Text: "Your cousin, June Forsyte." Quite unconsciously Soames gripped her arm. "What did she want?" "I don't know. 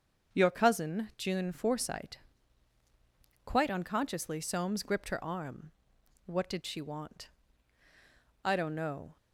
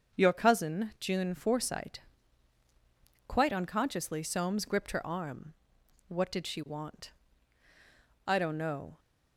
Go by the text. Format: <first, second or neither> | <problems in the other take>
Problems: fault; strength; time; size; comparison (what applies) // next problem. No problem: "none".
neither | starts louder than the rest; the same in both